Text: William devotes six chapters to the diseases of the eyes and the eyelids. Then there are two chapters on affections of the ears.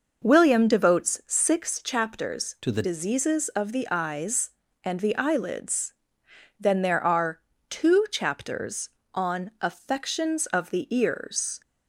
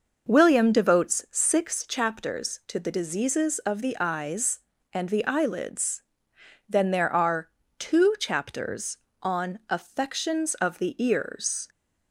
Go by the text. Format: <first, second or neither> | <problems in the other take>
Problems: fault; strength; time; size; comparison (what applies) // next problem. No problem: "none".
second | changes voice from "to" to "the"; from 2.6 to 2.8 s; 0.2 s long // pauses between "are" and "two"; slight; at 7.3 s; 0.30 s long; slight in the second